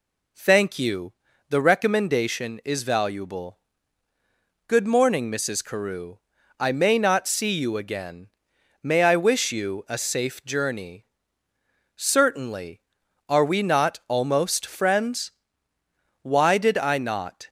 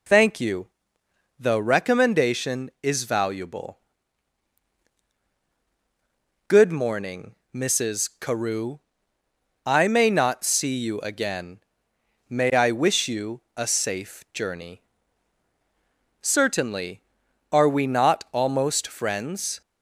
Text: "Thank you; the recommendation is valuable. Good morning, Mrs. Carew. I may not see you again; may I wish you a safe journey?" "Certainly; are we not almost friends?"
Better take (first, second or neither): second